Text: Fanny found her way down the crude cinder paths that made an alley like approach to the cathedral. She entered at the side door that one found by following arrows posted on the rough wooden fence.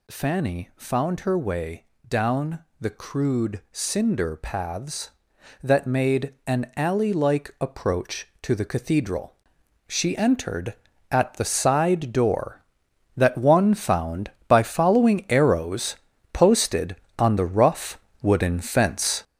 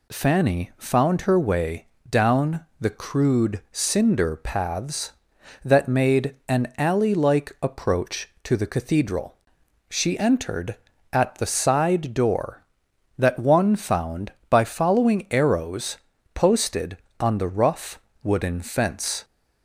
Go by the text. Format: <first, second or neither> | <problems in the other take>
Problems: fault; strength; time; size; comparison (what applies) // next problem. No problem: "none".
second | gets louder; strong; throughout; 7.5 dB // pauses between "way" and "down"; slight; at 1.8 s; 0.24 s long; slight in the second // pauses between "down" and "the"; slight; at 2.6 s; 0.16 s long // pauses between "arrows" and "posted"; slight; at 15.9 s; 0.36 s long; slight in the second // pauses between "rough" and "wooden"; slight; at 17.9 s; 0.24 s long; slight in the second